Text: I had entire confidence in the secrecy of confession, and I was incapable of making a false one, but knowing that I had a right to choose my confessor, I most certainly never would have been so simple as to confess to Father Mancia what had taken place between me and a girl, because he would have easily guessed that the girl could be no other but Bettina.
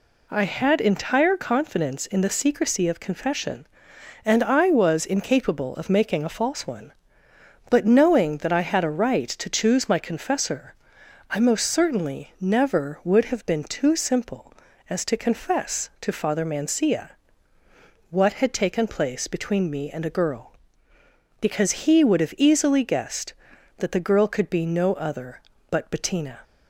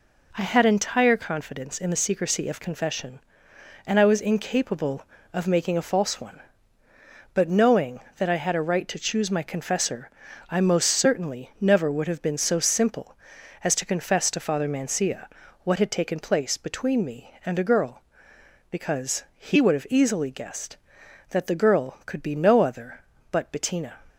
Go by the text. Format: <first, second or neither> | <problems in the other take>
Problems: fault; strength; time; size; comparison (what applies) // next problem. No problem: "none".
second | says "too" for "so"; at 13.6 s // pauses between "Mancia" and "what"; at 17.1 s; 1.0 s long; slight in the second